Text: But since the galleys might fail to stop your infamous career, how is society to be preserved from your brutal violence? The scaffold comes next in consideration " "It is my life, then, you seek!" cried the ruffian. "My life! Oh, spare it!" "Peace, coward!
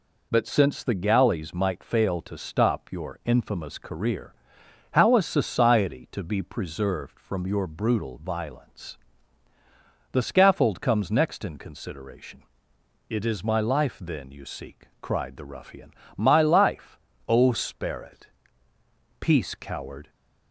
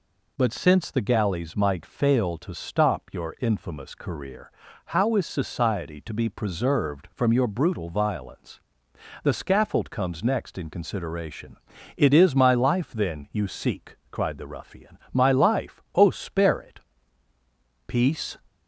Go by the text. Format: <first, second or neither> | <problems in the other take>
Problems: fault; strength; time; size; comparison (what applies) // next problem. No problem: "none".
first | stops before "coward"; at 18.4 s